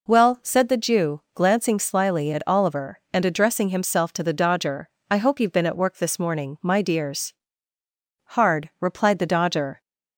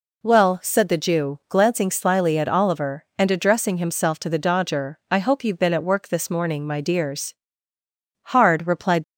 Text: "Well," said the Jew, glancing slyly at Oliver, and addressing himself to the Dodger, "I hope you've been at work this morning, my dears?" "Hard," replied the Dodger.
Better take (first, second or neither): first